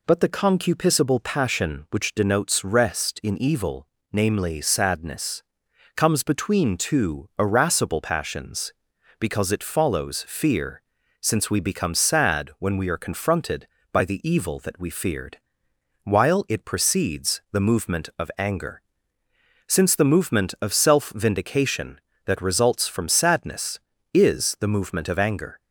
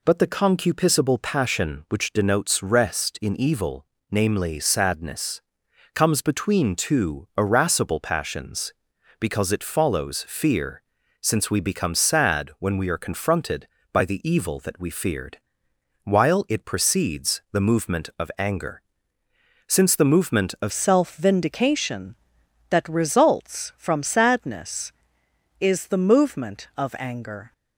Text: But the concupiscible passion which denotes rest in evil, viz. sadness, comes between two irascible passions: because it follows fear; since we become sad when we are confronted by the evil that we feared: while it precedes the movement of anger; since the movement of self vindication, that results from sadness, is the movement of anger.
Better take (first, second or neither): first